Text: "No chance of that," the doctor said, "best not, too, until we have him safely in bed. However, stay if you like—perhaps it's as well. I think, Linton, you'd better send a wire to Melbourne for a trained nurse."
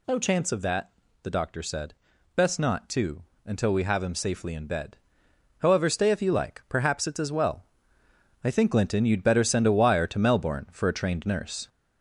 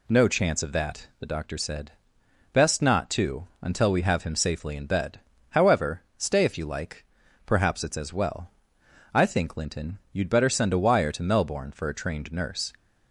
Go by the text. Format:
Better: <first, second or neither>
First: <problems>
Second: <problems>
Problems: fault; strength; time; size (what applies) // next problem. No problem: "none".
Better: second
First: gets louder; noticeable; throughout; 4 dB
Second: none